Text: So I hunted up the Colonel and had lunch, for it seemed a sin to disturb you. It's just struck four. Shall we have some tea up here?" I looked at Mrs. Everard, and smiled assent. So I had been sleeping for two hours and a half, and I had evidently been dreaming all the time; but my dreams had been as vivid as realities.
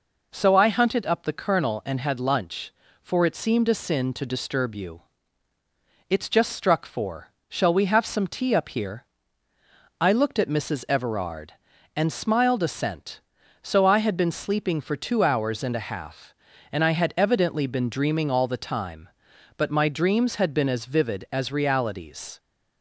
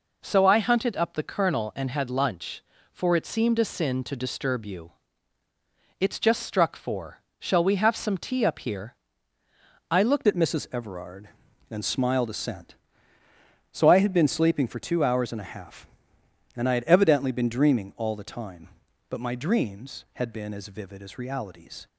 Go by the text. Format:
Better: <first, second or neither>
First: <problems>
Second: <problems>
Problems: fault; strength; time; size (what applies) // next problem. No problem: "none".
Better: first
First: none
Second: changes voice at "at"; from 10.2 s on; 11.6 s long